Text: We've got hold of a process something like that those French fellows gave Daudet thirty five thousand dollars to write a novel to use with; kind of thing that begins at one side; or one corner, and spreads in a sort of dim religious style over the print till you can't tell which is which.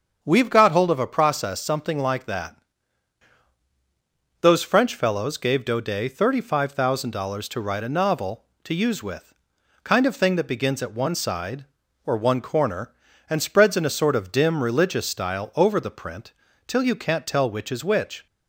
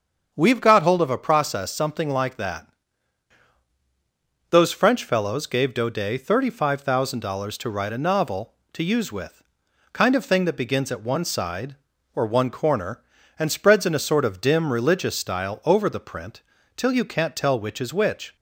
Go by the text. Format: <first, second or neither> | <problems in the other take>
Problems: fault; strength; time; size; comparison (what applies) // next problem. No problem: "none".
neither | starts louder than the rest; the same in both // pauses between "that" and "those"; strong; the same in both // pauses between "print" and "till"; slight; the same in both